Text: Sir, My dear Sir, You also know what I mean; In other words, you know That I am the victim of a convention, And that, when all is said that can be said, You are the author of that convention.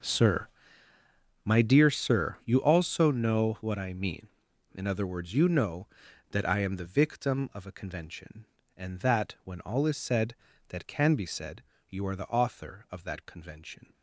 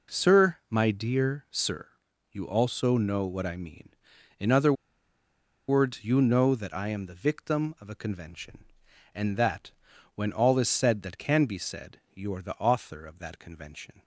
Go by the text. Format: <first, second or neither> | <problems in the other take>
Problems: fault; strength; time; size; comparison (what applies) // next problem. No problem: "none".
first | pauses between "other" and "words"; noticeable; at 4.7 s; 0.95 s long